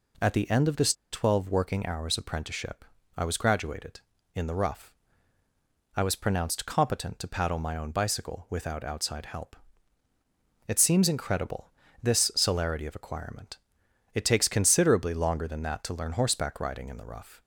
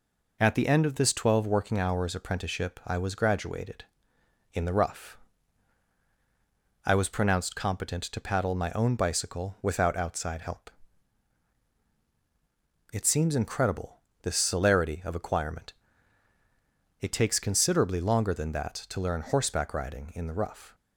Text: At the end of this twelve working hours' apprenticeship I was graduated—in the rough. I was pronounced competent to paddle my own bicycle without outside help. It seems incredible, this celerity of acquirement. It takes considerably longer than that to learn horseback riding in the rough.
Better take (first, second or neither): second